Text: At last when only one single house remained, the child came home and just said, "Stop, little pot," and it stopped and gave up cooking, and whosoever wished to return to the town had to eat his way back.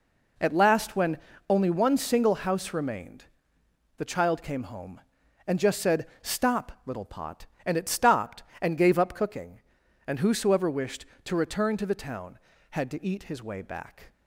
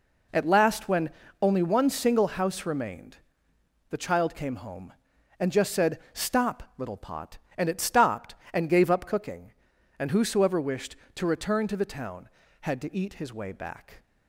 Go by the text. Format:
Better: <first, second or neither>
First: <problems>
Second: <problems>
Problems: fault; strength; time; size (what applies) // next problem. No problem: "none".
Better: neither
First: pauses between "when" and "only"; slight; at 1.1 s; 0.30 s long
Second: pauses between "when" and "only"; slight; at 1.1 s; 0.30 s long